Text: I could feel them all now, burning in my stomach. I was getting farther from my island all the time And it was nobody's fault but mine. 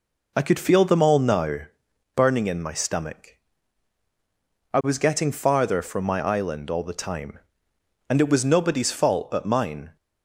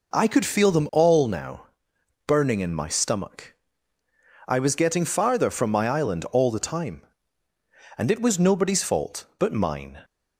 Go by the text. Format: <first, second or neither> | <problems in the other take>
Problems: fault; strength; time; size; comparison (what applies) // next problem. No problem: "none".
neither | none